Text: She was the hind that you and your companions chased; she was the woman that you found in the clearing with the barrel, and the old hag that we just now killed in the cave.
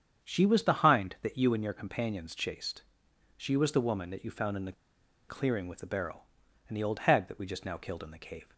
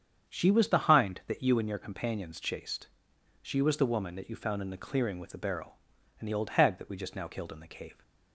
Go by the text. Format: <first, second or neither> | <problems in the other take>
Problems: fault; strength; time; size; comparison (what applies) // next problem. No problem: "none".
second | starts louder than the rest; strong; until 1.3 s; 8 dB; strong in the second // pauses between "the" and "clearing"; noticeable; at 4.7 s; 0.56 s long